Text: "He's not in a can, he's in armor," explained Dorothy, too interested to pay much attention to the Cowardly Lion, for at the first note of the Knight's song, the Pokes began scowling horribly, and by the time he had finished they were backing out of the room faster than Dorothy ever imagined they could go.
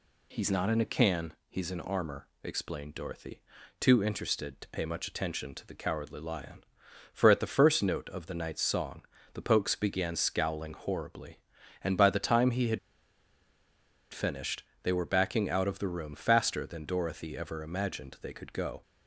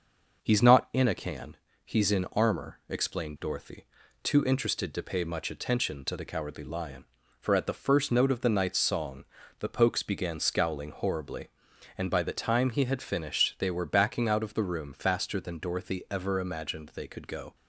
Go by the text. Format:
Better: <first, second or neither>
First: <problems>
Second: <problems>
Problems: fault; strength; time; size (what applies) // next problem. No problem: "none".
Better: second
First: pauses between "had" and "finished"; strong; at 12.7 s; 1.3 s long // pauses between "finished" and "they"; slight; at 14.6 s; 0.20 s long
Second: none